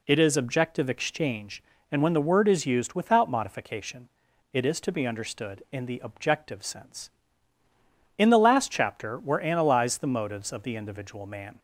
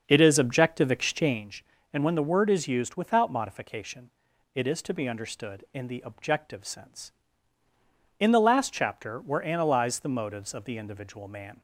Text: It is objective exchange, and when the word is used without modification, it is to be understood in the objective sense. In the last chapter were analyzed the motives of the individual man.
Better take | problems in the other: first | starts louder than the rest; until 1.5 s; 6.5 dB

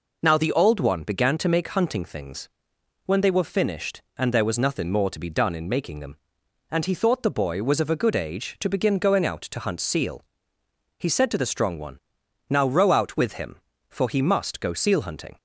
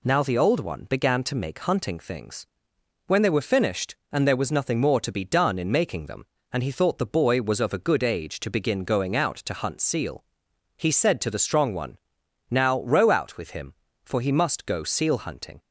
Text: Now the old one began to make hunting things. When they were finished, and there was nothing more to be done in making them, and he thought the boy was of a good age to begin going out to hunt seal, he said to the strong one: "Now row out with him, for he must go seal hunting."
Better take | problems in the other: neither | none

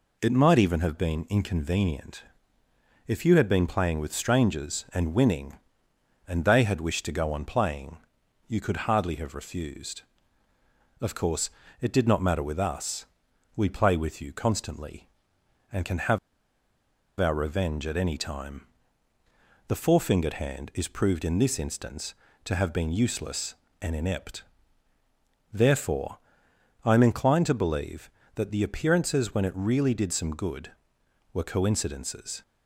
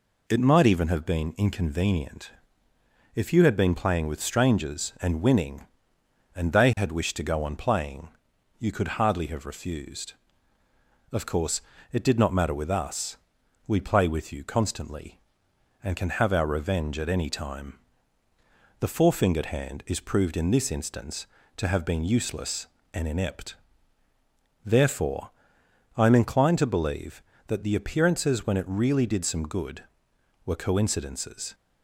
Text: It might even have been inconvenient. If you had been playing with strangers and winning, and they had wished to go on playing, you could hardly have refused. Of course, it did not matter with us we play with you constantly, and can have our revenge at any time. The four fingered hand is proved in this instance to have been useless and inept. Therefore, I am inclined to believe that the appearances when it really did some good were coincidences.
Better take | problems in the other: second | pauses between "us" and "we"; noticeable; at 13.0 s; 0.50 s long; noticeable in the second // pauses between "have" and "our"; at 16.1 s; 1.0 s long

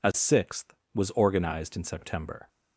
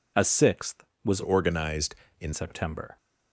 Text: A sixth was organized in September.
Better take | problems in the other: first | changes voice from "organized" to "in"; from 1.2 to 2.3 s; 1.1 s long

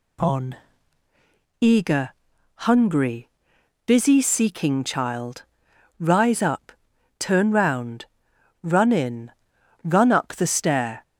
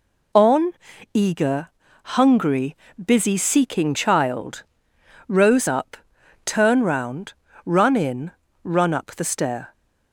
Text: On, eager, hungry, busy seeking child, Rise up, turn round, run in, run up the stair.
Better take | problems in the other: first | says "Rose" for "Rise"; at 5.2 s

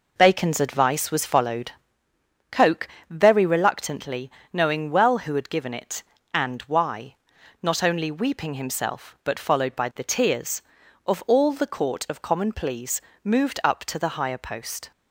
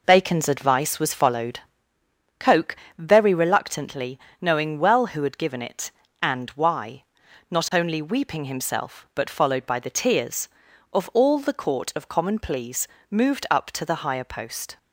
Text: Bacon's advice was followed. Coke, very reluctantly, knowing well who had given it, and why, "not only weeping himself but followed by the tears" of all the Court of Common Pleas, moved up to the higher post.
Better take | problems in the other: neither | none

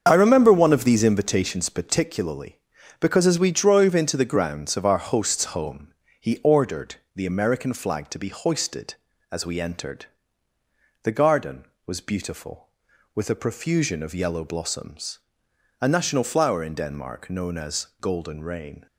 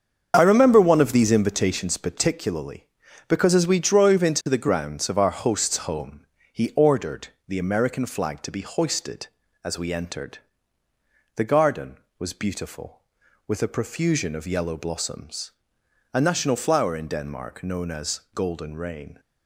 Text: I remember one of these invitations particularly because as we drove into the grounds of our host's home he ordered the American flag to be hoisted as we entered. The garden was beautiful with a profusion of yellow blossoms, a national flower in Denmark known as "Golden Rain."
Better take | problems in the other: neither | starts louder than the rest; the same in both // pauses between "home" and "he"; slight; the same in both // pauses between "ordered" and "the"; slight; the same in both

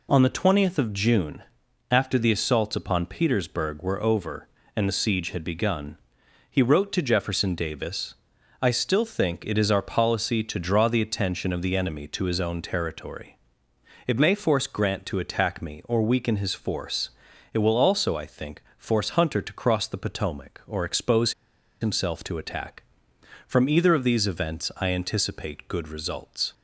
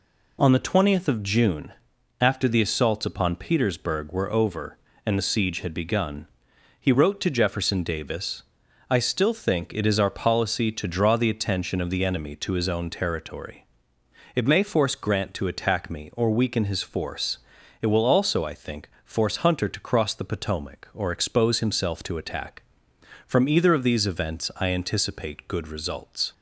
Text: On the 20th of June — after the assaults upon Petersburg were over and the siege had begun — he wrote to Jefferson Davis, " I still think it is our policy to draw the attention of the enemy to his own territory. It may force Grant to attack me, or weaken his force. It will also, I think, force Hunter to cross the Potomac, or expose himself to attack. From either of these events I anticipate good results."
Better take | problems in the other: second | pauses between "expose" and "himself"; noticeable; at 21.3 s; 0.47 s long

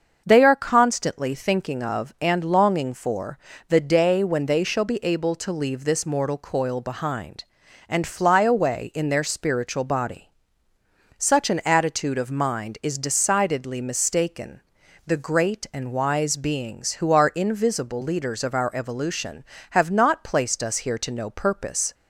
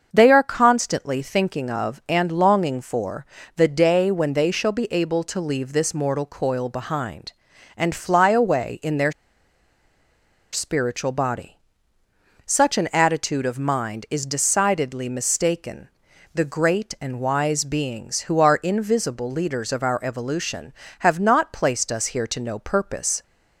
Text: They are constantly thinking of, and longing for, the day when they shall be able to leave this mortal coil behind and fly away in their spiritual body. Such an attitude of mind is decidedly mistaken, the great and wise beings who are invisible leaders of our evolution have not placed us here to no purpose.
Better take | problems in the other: first | starts louder than the rest; until 1.1 s; 6.5 dB; also in the first // pauses between "their" and "spiritual"; strong; at 9.1 s; 1.3 s long

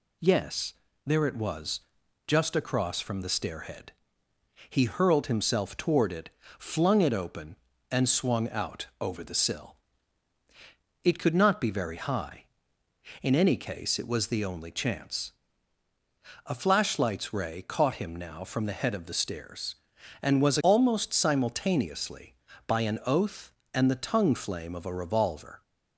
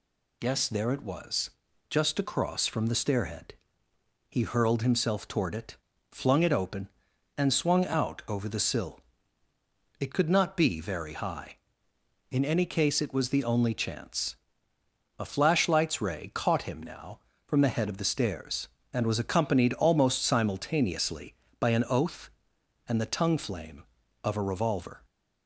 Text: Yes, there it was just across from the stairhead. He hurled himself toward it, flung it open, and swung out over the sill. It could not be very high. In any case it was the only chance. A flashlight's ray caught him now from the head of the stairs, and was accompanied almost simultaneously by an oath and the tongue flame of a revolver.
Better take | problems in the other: second | pauses between "was" and "just"; noticeable; at 1.8 s; 0.46 s long; also in the second // pauses between "out" and "over"; slight; at 8.8 s; 0.16 s long // skips "accompanied"; at 20.5 s

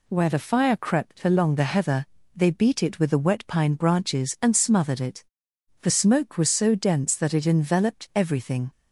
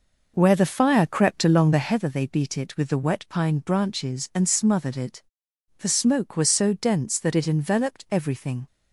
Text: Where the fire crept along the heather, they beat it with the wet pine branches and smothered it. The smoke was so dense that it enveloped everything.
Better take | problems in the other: first | starts louder than the rest; noticeable; until 2.0 s; 5 dB

